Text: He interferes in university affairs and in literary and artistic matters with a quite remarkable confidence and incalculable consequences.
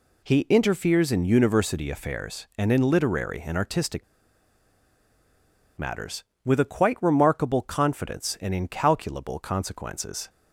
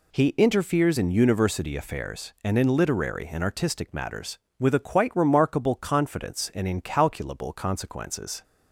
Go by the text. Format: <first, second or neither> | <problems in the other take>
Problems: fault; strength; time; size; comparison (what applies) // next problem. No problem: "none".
second | pauses between "artistic" and "matters"; strong; at 4.0 s; 1.7 s long